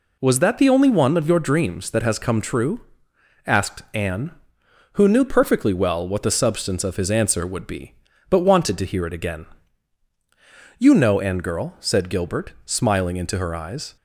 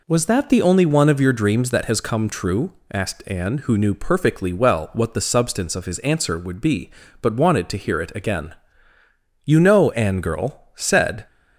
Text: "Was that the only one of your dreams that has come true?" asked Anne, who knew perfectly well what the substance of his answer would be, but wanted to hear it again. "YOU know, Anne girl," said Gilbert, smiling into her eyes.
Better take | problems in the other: first | stops before "Gilbert smiling into her eyes"; at 11.2 s

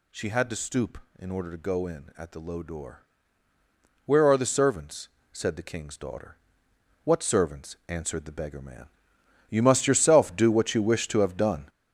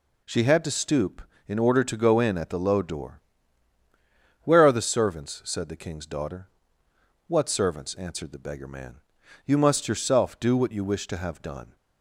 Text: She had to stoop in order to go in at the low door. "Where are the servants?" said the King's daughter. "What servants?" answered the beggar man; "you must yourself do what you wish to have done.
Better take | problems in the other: second | gets louder; strong; throughout; 8 dB

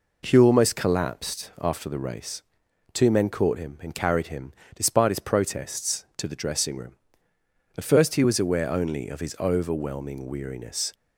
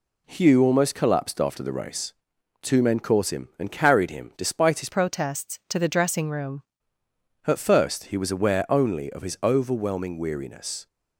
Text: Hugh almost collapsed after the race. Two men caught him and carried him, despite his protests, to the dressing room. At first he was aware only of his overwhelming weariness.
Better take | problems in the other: first | changes voice from "protests" to "room"; from 4.9 to 6.6 s; 1.7 s long

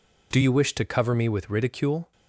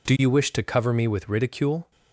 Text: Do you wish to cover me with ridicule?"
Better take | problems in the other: neither | none

